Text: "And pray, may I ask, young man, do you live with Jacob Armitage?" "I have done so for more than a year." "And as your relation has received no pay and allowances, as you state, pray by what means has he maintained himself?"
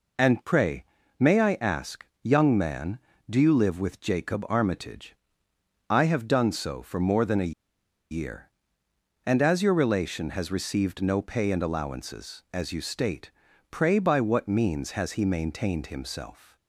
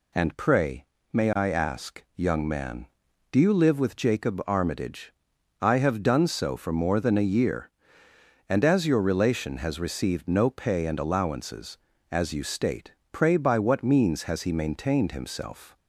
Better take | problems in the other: second | pauses between "a" and "year"; noticeable; at 7.5 s; 0.57 s long

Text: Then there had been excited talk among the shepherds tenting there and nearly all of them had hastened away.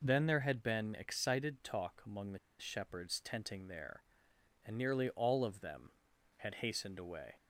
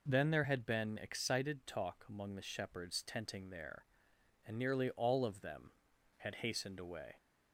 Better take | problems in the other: second | pauses between "the" and "shepherds"; slight; at 2.3 s; 0.21 s long

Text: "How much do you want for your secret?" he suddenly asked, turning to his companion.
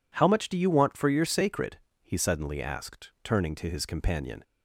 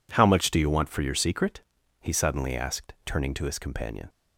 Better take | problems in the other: second | says "sacred" for "secret"; at 1.2 s

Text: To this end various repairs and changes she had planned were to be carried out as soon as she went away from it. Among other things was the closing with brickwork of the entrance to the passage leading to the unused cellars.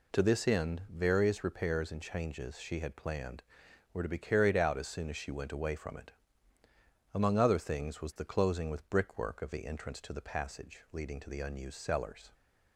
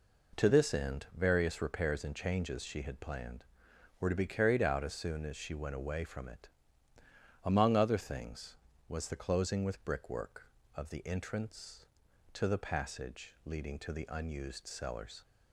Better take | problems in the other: neither | none

